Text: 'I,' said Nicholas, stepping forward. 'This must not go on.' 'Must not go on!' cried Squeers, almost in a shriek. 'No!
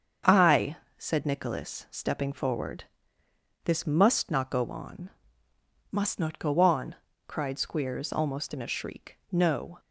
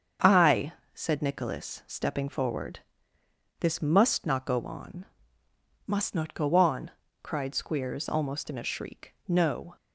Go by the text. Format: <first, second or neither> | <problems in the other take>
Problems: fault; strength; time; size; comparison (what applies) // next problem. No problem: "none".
neither | starts louder than the rest; the same in both